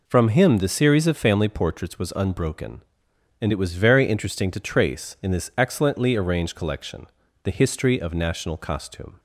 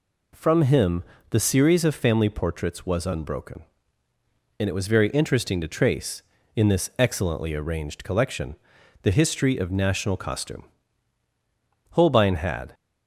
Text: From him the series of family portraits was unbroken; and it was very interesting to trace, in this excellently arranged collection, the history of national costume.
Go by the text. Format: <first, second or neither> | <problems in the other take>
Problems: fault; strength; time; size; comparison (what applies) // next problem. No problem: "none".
first | pauses between "him" and "the"; slight; at 1.0 s; 0.26 s long // goes on to say "Holbein had"; noticeable; from 11.9 s on; 0.82 s long